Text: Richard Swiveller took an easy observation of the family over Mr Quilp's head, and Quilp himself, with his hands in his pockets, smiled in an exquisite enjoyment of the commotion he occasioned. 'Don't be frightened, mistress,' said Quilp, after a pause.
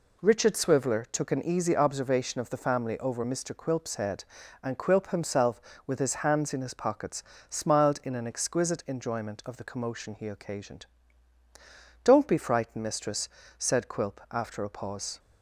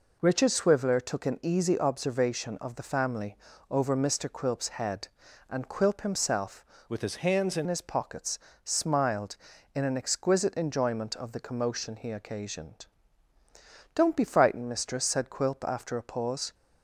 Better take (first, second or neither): first